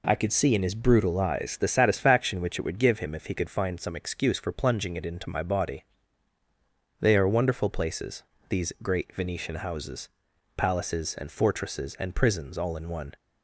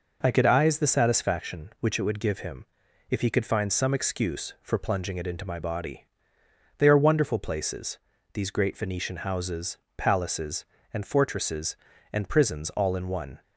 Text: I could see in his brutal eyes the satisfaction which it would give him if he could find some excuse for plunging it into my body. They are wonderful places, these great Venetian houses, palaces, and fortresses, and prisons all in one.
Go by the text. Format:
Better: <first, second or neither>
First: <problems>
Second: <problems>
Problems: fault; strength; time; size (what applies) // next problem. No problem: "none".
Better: first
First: none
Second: skips "see in his brutal"; at 0.4 s // pauses between "him" and "if"; at 2.6 s; 0.44 s long